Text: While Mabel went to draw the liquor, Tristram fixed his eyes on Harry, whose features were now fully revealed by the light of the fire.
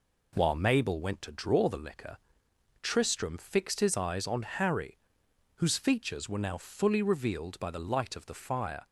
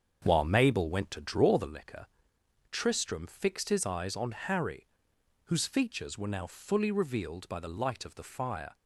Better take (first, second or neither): first